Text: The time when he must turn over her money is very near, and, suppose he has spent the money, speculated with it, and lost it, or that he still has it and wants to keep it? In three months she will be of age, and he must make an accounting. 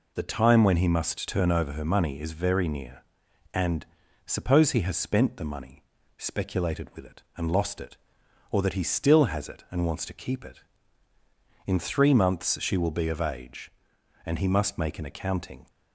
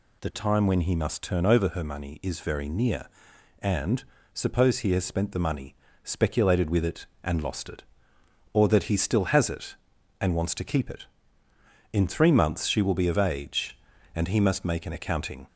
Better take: neither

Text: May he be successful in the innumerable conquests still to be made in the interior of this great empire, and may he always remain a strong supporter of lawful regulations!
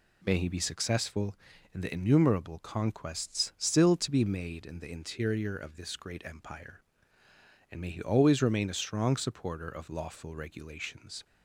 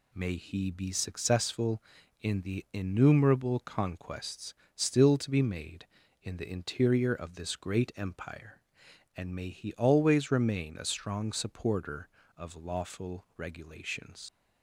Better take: first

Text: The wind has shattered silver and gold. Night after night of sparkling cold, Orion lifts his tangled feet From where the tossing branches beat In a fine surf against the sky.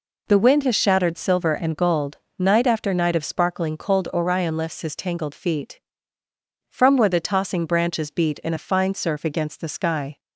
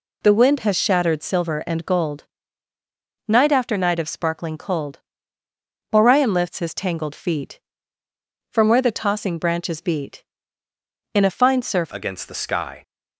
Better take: first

